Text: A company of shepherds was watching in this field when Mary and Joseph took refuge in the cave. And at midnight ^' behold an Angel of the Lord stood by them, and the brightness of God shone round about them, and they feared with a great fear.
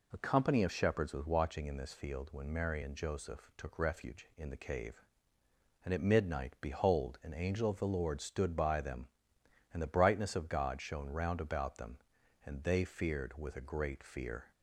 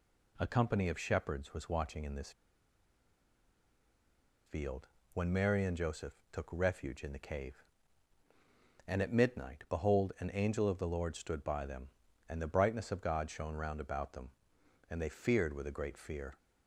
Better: first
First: none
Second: pauses between "this" and "field"; strong; at 2.3 s; 2.1 s long // pauses between "field" and "when"; slight; at 4.8 s; 0.26 s long // pauses between "Joseph" and "took"; slight; at 6.1 s; 0.18 s long

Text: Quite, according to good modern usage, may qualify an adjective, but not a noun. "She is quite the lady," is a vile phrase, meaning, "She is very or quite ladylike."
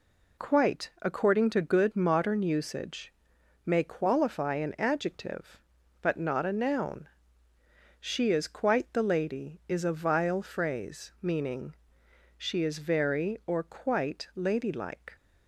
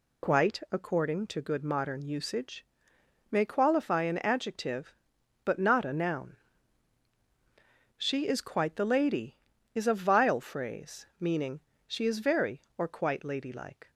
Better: neither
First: none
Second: none

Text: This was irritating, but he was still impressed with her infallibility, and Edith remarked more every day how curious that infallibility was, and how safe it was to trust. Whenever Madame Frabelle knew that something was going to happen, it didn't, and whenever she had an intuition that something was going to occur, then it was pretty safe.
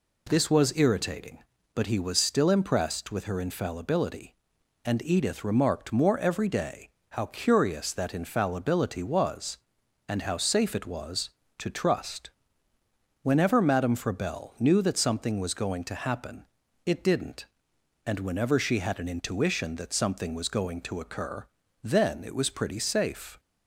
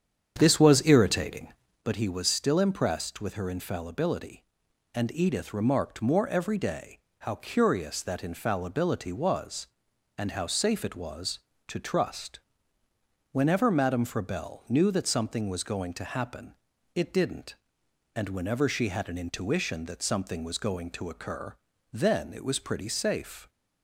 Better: first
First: pauses between "day" and "how"; slight; at 6.8 s; 0.22 s long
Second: starts louder than the rest; strong; until 1.9 s; 8 dB // pauses between "day" and "how"; slight; at 6.9 s; 0.22 s long

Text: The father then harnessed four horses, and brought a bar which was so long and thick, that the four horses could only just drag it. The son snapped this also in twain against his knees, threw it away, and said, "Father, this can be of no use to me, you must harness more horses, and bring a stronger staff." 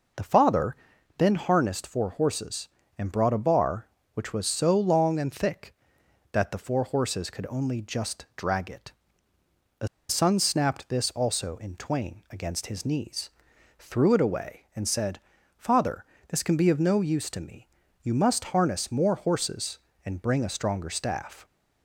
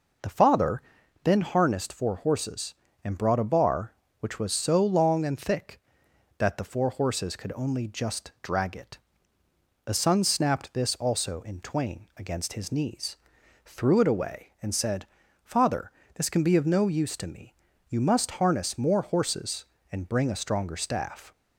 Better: second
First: pauses between "father" and "then"; at 0.7 s; 0.42 s long // pauses between "The" and "son"; slight; at 9.8 s; 0.21 s long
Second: pauses between "father" and "then"; at 0.8 s; 0.42 s long

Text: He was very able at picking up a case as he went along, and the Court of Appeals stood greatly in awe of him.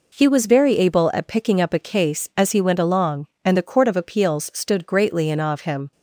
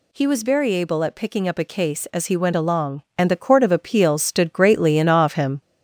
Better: first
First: none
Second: gets louder; noticeable; throughout; 4 dB

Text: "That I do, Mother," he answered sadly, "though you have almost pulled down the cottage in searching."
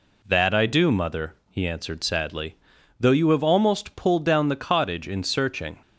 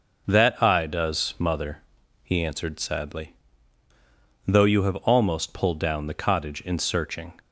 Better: first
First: none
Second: says "does" for "do"; at 0.8 s

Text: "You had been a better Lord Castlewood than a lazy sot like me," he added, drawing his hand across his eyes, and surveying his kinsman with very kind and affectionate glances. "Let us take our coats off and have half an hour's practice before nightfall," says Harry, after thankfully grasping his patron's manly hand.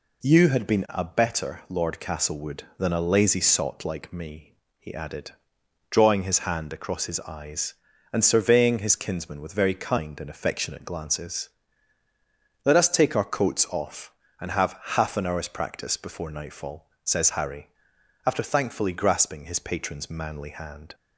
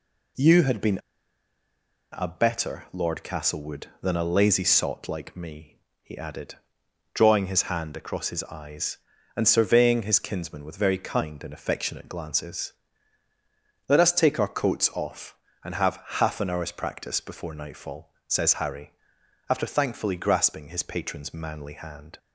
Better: first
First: pauses between "have" and "half"; slight; at 14.7 s; 0.18 s long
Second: pauses between "been" and "a"; at 0.9 s; 1.1 s long // pauses between "have" and "half"; slight; at 16.0 s; 0.18 s long

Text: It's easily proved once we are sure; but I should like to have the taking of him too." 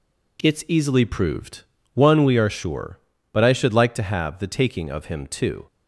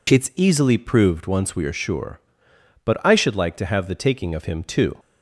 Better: second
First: says "one" for "once"; at 1.9 s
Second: none

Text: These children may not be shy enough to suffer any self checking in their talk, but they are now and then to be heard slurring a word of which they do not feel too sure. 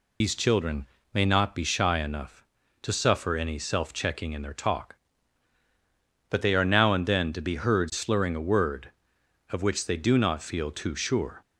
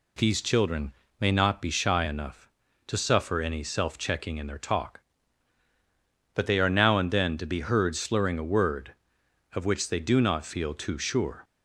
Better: second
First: loses the start of "These"; at 0.2 s; 105 ms // pauses between "children" and "may"; slight; at 0.8 s; 0.26 s long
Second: pauses between "children" and "may"; slight; at 0.9 s; 0.26 s long

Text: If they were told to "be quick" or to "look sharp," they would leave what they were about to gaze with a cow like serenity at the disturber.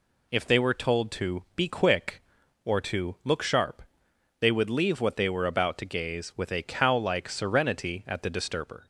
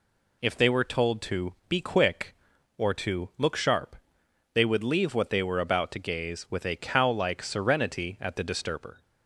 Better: neither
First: none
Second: none

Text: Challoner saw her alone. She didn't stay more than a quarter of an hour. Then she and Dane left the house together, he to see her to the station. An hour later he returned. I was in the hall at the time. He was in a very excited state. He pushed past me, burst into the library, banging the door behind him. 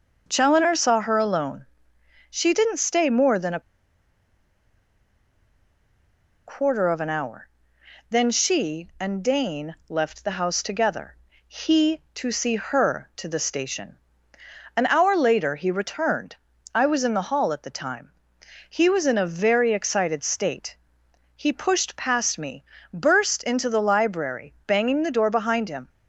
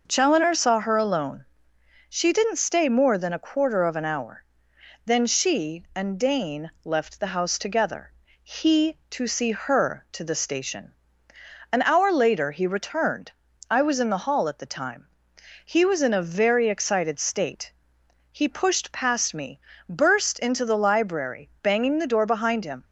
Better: second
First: pauses between "a" and "quarter"; strong; at 3.5 s; 2.8 s long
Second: none

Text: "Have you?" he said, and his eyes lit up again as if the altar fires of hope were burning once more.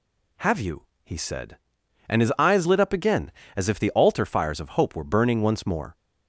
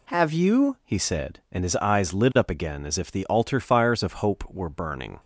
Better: first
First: none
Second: stops before "once more"; at 5.1 s

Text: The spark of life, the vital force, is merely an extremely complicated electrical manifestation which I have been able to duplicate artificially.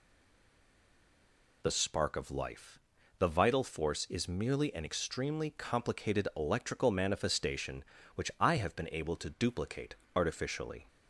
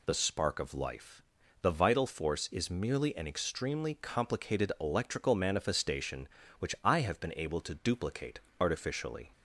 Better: second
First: stays silent before the first word; noticeable; until 1.6 s; 1.6 s long // pauses between "duplicate" and "artificially"; slight; at 9.9 s; 0.22 s long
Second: pauses between "duplicate" and "artificially"; slight; at 8.3 s; 0.22 s long

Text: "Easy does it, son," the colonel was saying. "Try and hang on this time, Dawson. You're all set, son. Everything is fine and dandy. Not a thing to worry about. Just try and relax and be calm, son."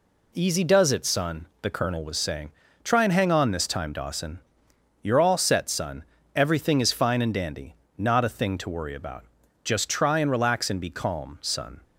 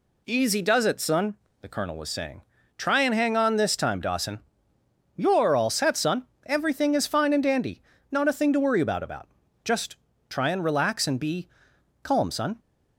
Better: first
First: none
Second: says "about" twice; at 9.0 s // pauses between "Just" and "try"; slight; at 9.9 s; 0.34 s long // pauses between "be" and "calm"; noticeable; at 11.4 s; 0.56 s long

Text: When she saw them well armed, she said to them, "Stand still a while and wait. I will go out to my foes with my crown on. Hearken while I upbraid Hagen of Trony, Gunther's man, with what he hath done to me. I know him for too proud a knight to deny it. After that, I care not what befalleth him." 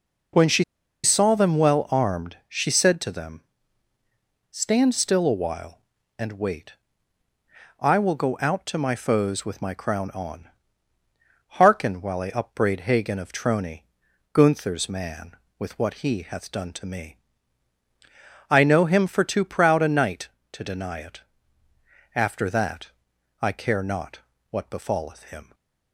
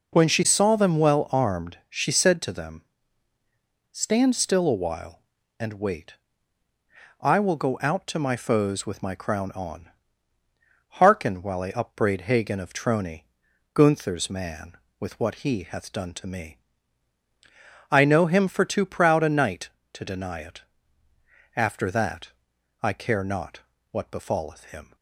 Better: second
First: pauses between "she" and "saw"; at 0.6 s; 0.40 s long // pauses between "not" and "what"; slight; at 24.1 s; 0.32 s long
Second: pauses between "not" and "what"; slight; at 23.5 s; 0.32 s long

